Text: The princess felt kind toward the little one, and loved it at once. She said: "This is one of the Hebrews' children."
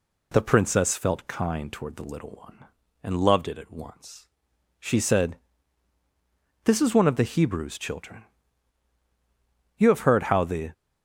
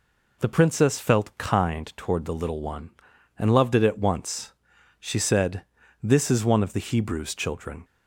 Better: second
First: goes on to say "You have heard how the"; noticeable; from 9.7 s on; 0.96 s long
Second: none

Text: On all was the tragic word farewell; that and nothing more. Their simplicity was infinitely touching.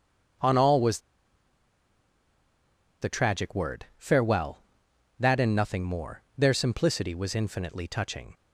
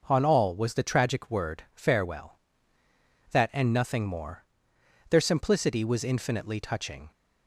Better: second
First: starts louder than the rest; until 3.4 s; 6.5 dB // pauses between "was" and "the"; strong; at 0.9 s; 2.0 s long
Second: none

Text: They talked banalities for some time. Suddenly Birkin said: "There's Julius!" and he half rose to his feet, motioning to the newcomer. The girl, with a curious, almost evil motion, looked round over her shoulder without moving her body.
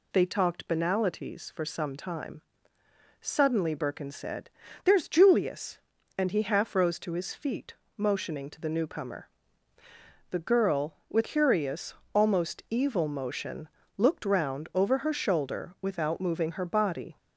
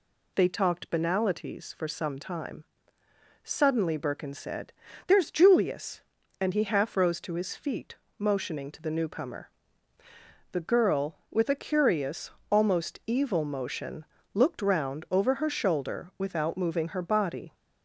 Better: second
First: skips "a"; at 11.2 s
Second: none

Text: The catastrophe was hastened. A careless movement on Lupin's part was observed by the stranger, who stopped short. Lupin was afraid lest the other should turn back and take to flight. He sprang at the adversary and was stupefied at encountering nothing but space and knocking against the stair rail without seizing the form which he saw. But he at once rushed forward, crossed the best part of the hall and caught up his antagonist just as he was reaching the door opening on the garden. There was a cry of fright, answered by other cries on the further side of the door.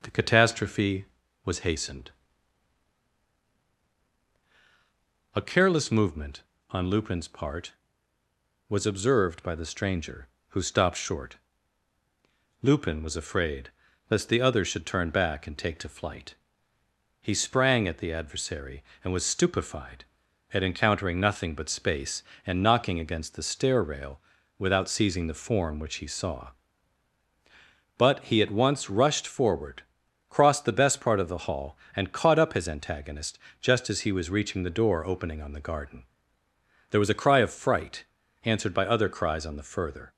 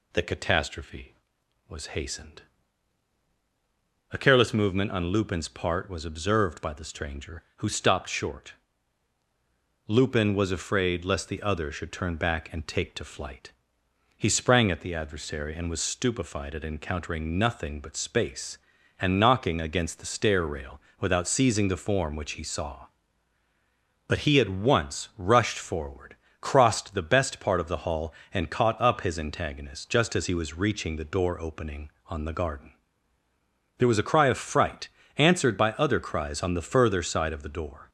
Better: second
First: pauses between "afraid" and "lest"; at 13.6 s; 0.40 s long // pauses between "rail" and "without"; at 24.1 s; 0.38 s long // pauses between "antagonist" and "just"; slight; at 33.3 s; 0.24 s long // stops before "side of the door"; at 40.1 s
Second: pauses between "rail" and "without"; slight; at 20.8 s; 0.18 s long

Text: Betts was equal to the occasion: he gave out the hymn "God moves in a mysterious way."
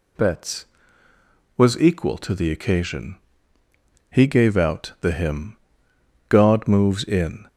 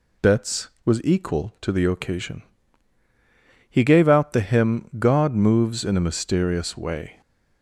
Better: second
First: pauses between "hymn" and "God"; noticeable; at 5.5 s; 0.72 s long // stops before "a mysterious way"; at 7.4 s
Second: none

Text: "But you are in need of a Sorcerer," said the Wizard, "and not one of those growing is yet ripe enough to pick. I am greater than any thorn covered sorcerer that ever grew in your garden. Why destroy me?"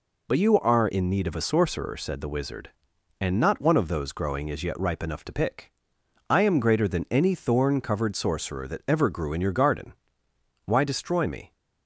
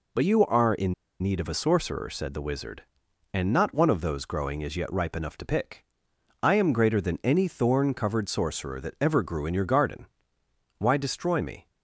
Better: first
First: none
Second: pauses between "in" and "need"; slight; at 0.9 s; 0.28 s long

